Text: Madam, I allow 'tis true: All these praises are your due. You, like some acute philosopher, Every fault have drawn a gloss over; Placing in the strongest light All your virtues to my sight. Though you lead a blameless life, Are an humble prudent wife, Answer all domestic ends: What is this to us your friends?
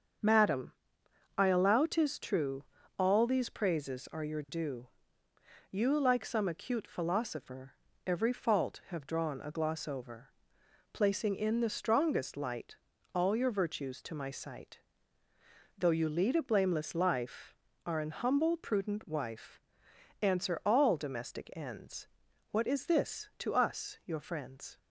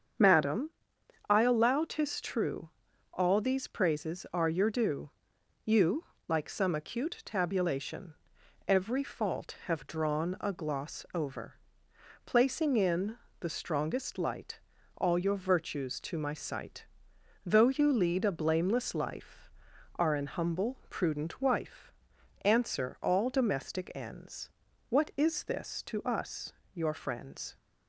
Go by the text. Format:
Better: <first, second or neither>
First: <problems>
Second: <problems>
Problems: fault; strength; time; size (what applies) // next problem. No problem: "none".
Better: first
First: starts louder than the rest; until 1.8 s; 7 dB // pauses between "light" and "All"; slight; at 12.7 s; 0.36 s long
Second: starts louder than the rest; strong; until 1.7 s; 7.5 dB // says "tabulation" for "philosopher"; at 7.2 s // pauses between "in" and "the"; slight; at 13.1 s; 0.24 s long // pauses between "light" and "All"; at 14.5 s; 0.38 s long // pauses between "us" and "your"; slight; at 26.5 s; 0.18 s long